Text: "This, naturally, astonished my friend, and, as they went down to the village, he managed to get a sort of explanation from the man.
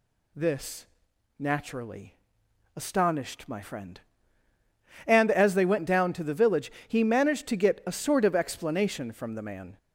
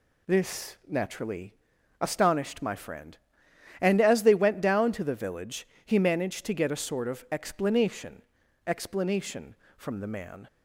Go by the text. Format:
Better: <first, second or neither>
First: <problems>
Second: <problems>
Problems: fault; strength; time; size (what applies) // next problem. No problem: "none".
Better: first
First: none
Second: says "explanation" twice; at 8.6 s